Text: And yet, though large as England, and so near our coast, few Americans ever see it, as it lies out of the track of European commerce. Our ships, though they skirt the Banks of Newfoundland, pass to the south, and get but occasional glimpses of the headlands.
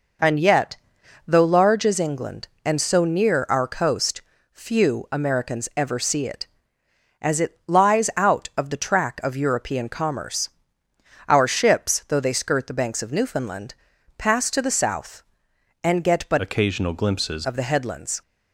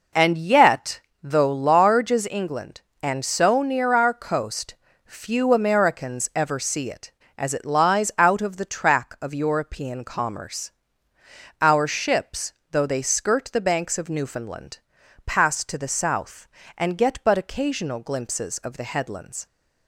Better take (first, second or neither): second